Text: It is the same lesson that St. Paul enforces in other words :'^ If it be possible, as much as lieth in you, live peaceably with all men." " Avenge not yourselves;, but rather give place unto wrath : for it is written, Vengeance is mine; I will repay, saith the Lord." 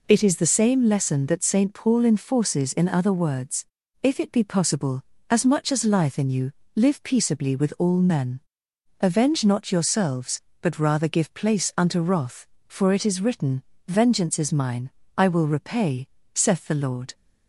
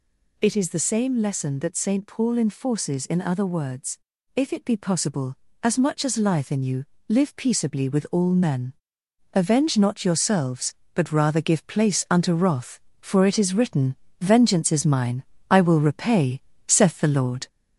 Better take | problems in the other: first | gets louder; noticeable; throughout; 4.5 dB

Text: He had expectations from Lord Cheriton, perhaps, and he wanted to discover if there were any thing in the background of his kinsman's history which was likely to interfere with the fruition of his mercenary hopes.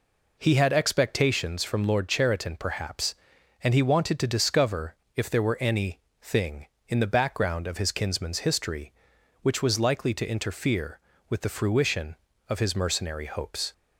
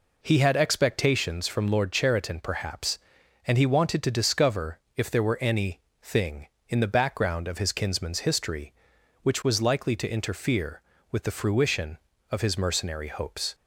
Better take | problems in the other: neither | pauses between "discover" and "if"; slight; the same in both // pauses between "any" and "thing"; slight; the same in both

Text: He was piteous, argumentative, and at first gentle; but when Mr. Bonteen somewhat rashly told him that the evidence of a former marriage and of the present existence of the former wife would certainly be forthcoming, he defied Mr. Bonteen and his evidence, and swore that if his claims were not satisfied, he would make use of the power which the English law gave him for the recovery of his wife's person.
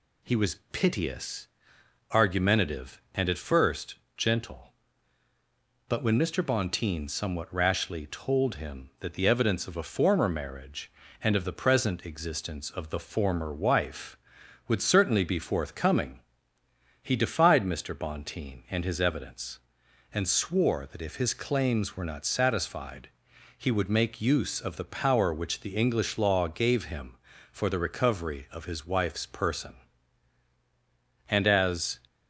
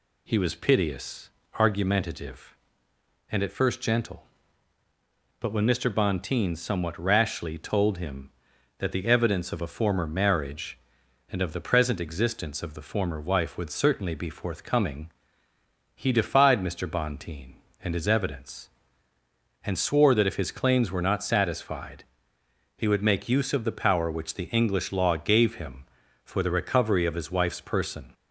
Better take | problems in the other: second | pauses between "first" and "gentle"; slight; at 3.9 s; 0.20 s long // goes on to say "And as"; noticeable; from 31.2 s on; 0.72 s long

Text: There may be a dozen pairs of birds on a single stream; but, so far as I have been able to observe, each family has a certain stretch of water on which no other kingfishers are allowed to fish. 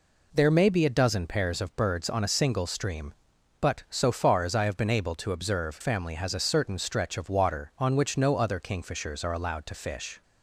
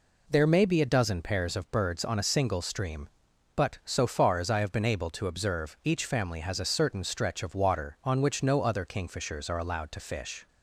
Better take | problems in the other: second | skips "each"; at 5.8 s

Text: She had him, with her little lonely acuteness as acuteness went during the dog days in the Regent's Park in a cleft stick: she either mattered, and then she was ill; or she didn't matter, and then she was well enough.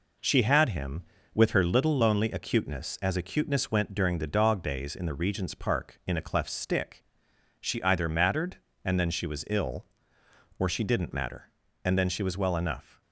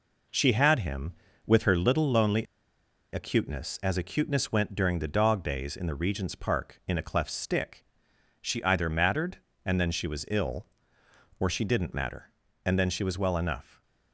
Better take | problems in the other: first | pauses between "lonely" and "acuteness"; noticeable; at 2.4 s; 0.68 s long // stays silent after the last word; slight; from 13.6 s on; 0.5 s long

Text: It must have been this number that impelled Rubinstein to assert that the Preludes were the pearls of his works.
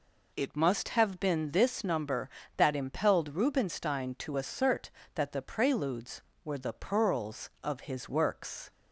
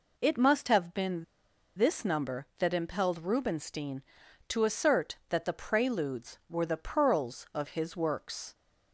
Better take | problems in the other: first | pauses between "been" and "this"; noticeable; at 1.2 s; 0.53 s long

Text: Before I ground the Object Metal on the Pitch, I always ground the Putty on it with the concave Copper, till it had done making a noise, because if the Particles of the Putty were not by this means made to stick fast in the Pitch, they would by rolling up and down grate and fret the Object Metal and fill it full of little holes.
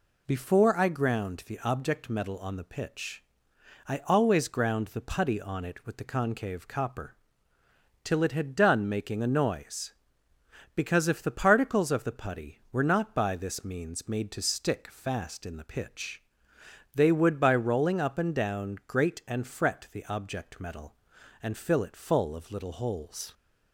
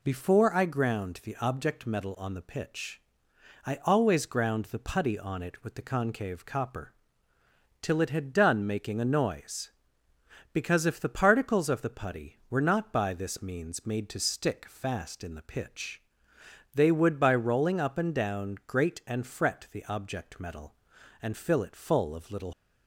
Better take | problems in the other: first | stops before "holes"; at 22.5 s

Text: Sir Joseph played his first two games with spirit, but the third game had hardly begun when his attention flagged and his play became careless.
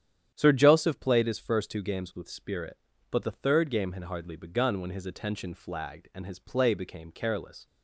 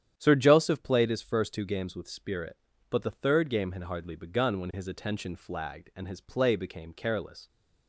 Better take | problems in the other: neither | starts louder than the rest; strong; the same in both

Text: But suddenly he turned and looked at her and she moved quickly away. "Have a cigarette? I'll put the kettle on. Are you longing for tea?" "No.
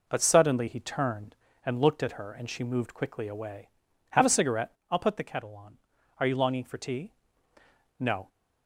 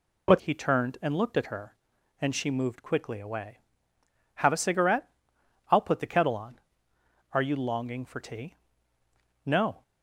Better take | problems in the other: first | skips "suddenly"; at 0.3 s

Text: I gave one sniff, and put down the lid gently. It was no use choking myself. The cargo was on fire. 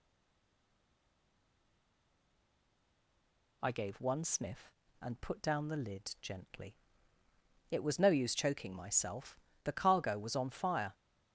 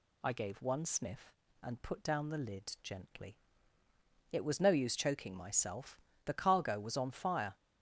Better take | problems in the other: second | stays silent before the first word; strong; until 3.6 s; 3.6 s long

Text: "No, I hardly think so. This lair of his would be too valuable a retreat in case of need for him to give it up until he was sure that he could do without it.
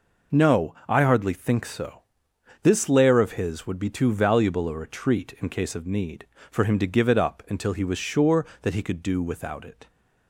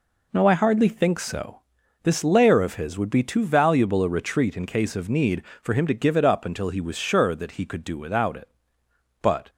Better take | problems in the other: first | goes on to say "But"; slight; from 9.2 s on; 0.26 s long

